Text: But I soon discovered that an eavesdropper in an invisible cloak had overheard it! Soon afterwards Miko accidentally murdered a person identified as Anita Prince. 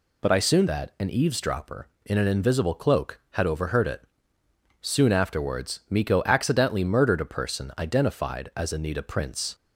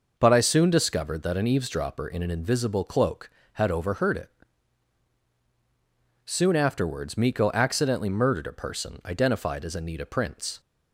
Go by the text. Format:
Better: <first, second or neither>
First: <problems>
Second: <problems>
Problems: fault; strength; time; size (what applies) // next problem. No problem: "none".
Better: second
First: skips "discovered"; at 0.6 s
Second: none